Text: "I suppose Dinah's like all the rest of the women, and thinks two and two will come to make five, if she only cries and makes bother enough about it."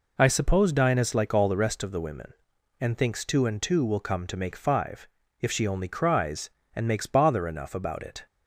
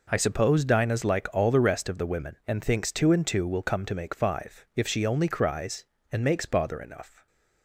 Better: first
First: none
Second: stops before "about it"; at 7.2 s

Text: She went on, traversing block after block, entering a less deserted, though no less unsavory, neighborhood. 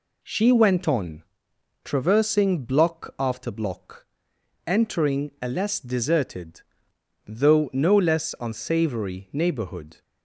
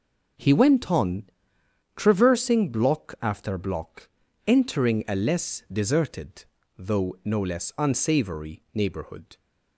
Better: first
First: none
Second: starts louder than the rest; noticeable; until 2.1 s; 6 dB // says "He" for "She"; at 0.3 s

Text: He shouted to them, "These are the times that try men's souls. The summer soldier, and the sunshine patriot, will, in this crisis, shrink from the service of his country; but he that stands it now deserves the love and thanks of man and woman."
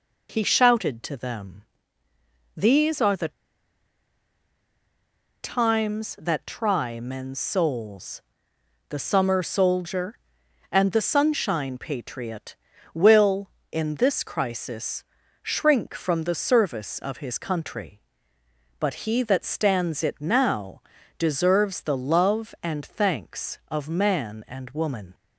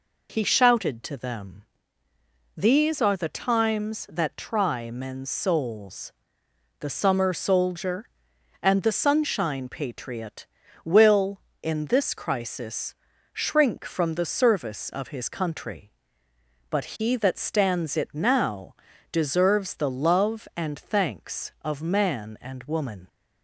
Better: second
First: pauses between "the" and "times"; strong; at 3.3 s; 2.1 s long // pauses between "now" and "deserves"; at 20.7 s; 0.38 s long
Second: pauses between "now" and "deserves"; at 18.7 s; 0.38 s long

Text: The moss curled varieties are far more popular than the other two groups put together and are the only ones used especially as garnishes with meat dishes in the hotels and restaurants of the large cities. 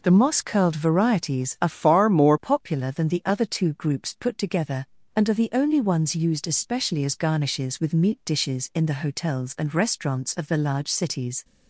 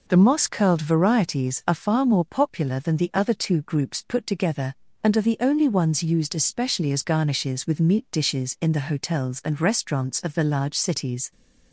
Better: second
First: changes voice from "far" to "more"; from 1.7 to 2.3 s; 0.6 s long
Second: none

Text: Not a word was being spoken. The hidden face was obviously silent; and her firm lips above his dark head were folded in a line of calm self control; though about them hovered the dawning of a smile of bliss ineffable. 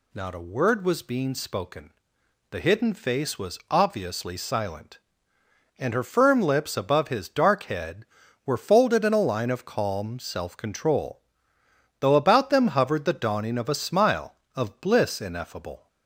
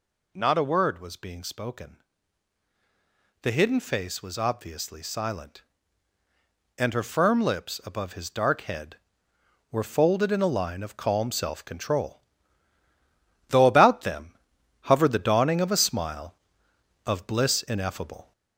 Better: first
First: none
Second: gets louder; slight; throughout; 3 dB // pauses between "them" and "hovered"; noticeable; at 14.3 s; 0.46 s long

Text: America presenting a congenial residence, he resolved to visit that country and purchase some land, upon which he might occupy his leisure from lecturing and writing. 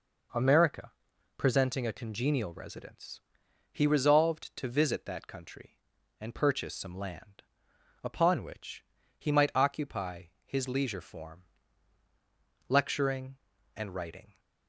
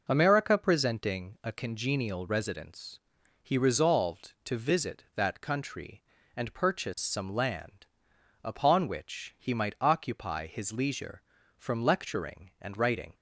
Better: second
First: pauses between "America" and "presenting"; at 0.9 s; 0.45 s long // pauses between "which" and "he"; slight; at 8.8 s; 0.34 s long // pauses between "occupy" and "his"; slight; at 10.2 s; 0.22 s long // says "form" for "from"; at 11.0 s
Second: none

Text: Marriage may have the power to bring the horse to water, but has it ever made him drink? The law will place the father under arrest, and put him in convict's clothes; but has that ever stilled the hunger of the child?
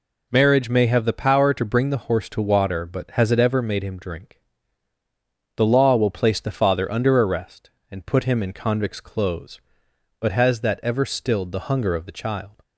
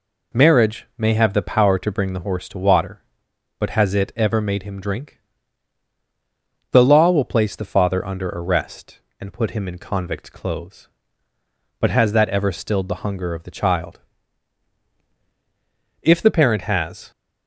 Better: first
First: none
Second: goes on to say "If the parent has"; noticeable; from 16.0 s on; 1.1 s long

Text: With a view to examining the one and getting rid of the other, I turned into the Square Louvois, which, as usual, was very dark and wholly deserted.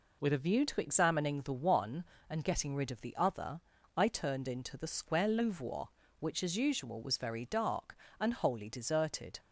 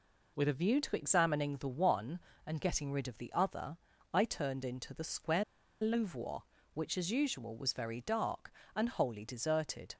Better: first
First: none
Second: pauses between "Square" and "Louvois"; at 5.4 s; 0.39 s long

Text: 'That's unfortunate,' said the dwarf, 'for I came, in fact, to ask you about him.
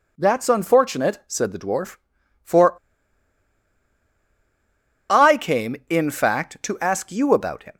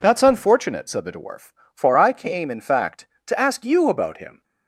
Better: second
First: pauses between "for" and "I"; strong; at 2.7 s; 2.3 s long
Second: none

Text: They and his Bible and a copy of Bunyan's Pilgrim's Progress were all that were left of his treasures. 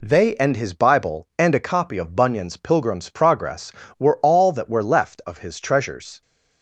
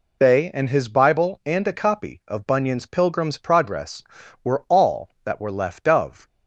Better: first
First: none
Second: stops before "his treasures"; at 6.2 s

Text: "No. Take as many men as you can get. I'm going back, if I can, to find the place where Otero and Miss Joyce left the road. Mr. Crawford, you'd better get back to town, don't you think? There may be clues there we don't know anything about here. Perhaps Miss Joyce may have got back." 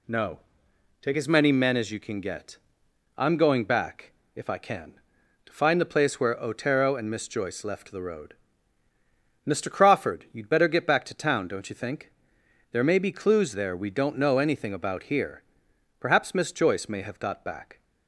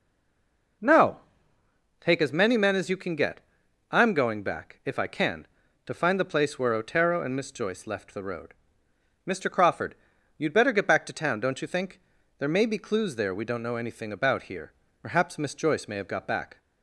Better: first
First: none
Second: stays silent before the first word; slight; until 0.8 s; 0.8 s long

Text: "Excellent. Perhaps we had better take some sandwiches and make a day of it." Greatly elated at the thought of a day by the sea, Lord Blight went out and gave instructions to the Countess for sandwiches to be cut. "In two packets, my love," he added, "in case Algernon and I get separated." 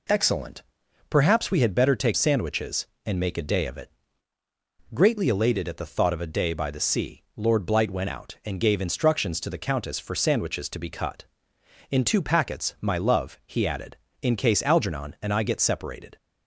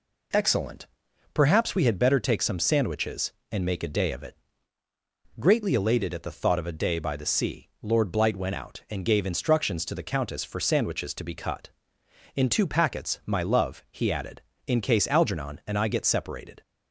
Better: second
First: skips "some"; at 2.1 s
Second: none

